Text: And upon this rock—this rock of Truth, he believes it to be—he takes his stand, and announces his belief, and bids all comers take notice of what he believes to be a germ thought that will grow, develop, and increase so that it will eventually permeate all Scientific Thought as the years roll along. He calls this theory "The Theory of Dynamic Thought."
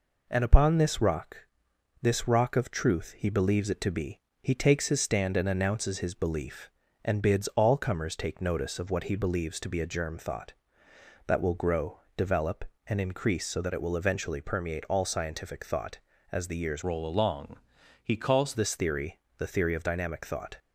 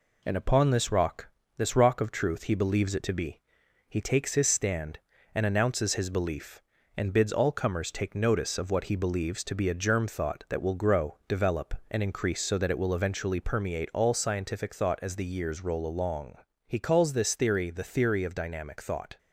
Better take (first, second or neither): second